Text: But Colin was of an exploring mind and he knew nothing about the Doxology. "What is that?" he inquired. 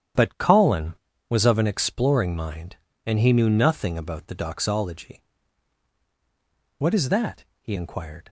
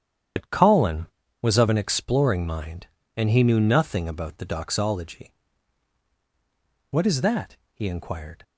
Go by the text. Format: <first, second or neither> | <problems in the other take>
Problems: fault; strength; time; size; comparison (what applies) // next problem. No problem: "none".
first | loses the start of "But"; at 0.3 s; 85 ms // starts louder than the rest; strong; until 1.7 s; 9.5 dB; strong in the first